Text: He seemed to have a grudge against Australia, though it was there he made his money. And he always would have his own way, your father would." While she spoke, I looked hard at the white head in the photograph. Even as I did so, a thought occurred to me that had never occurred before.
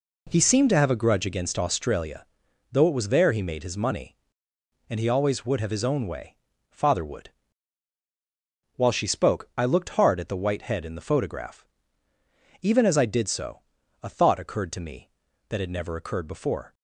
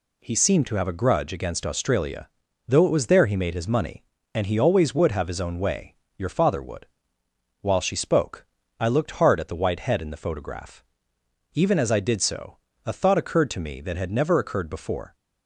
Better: second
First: skips "your"; at 6.5 s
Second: none

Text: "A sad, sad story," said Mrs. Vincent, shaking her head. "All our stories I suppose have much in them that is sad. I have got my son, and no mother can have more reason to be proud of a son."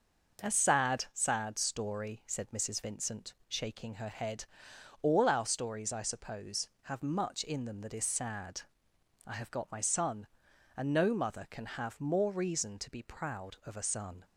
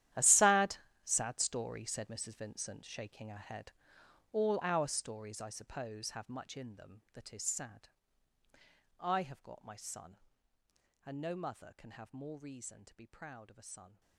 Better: first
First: starts louder than the rest; noticeable; until 1.4 s; 6 dB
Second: gets quieter; strong; throughout; 17 dB // starts louder than the rest; strong; until 1.4 s; 12 dB

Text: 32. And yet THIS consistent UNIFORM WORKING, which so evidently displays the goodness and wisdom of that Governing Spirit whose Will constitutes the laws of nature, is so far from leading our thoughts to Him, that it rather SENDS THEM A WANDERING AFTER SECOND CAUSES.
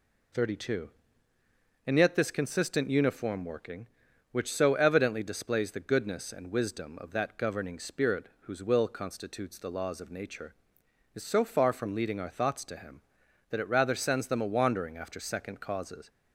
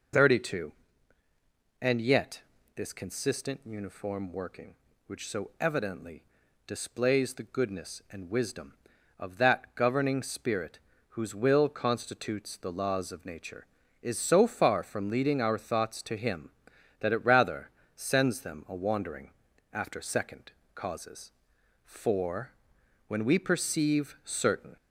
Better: first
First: none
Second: pauses between "yet" and "THIS"; slight; at 2.4 s; 0.34 s long // pauses between "evidently" and "displays"; noticeable; at 6.2 s; 0.46 s long // pauses between "Spirit" and "whose"; slight; at 10.7 s; 0.30 s long // pauses between "rather" and "SENDS"; slight; at 17.7 s; 0.26 s long // pauses between "WANDERING" and "AFTER"; at 19.3 s; 0.42 s long // pauses between "SECOND" and "CAUSES"; slight; at 20.5 s; 0.24 s long // goes on to say "For when we perceive certain"; strong; from 21.8 s on; 2.9 s long

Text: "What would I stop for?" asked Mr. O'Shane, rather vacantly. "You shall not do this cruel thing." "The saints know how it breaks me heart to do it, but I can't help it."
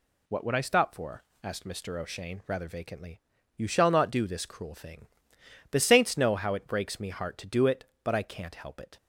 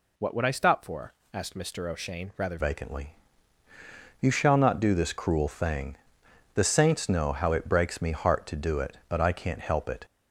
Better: first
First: none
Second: changes voice at "vacantly"; from 2.5 s on; 7.5 s long

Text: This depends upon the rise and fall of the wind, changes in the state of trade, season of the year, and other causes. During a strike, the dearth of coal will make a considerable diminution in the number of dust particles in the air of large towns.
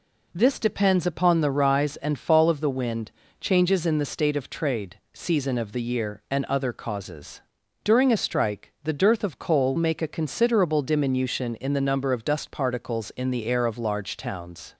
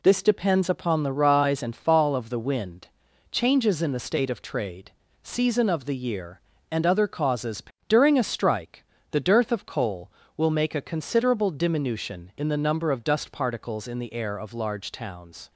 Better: second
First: skips "will"; at 9.7 s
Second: none

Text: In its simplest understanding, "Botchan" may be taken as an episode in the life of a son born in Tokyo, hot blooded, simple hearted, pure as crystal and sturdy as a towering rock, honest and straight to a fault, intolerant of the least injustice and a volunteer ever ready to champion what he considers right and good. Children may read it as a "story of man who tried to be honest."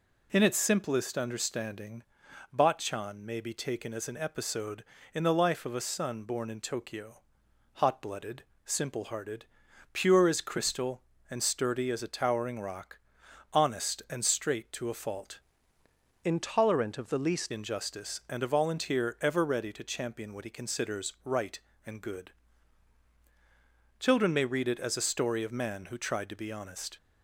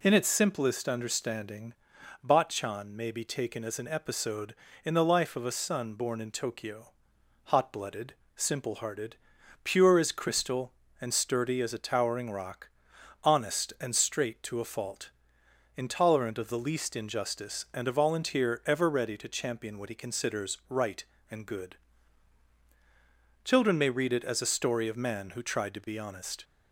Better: second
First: changes voice from "intolerant" to "least"; from 16.2 to 17.5 s; 1.3 s long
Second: none

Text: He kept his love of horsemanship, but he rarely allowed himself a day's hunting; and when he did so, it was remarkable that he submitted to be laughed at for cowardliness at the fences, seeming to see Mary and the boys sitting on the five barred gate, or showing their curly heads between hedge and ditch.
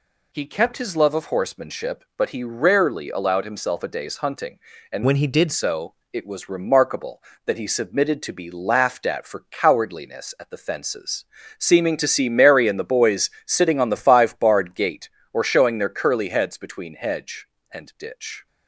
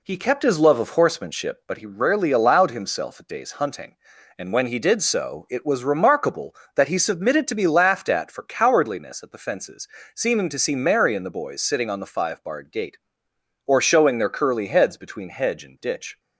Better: second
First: changes voice from "when" to "did"; from 5.0 to 5.5 s; 0.5 s long // pauses between "boys" and "sitting"; slight; at 13.3 s; 0.16 s long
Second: none

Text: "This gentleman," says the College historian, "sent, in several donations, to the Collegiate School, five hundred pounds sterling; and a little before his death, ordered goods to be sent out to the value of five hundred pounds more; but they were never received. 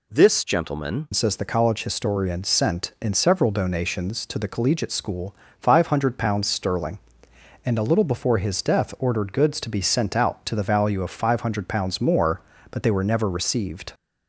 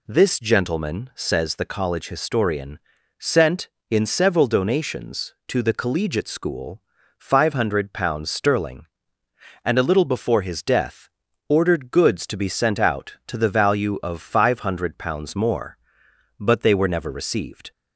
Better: second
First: changes voice at "says"; from 1.1 s on; 12.8 s long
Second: none

